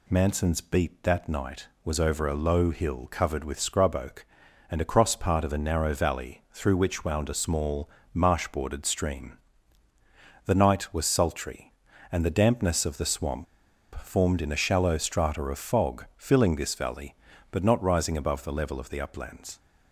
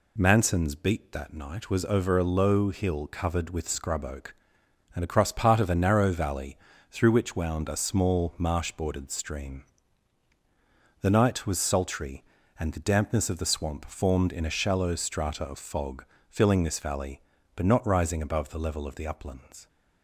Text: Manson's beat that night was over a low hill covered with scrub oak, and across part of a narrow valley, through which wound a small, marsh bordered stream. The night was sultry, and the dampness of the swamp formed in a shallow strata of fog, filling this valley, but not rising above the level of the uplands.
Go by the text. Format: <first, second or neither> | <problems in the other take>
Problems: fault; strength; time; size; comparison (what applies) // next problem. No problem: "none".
second | pauses between "swamp" and "formed"; noticeable; at 13.4 s; 0.54 s long